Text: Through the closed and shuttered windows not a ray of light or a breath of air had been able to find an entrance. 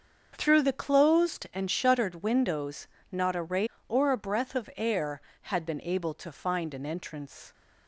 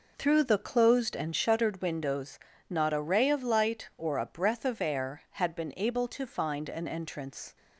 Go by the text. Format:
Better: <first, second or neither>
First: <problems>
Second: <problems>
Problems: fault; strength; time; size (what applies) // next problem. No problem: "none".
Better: second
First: starts louder than the rest; until 1.3 s; 6.5 dB // pauses between "windows" and "not"; slight; at 2.8 s; 0.24 s long // skips "of light"; at 3.7 s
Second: pauses between "windows" and "not"; slight; at 2.3 s; 0.32 s long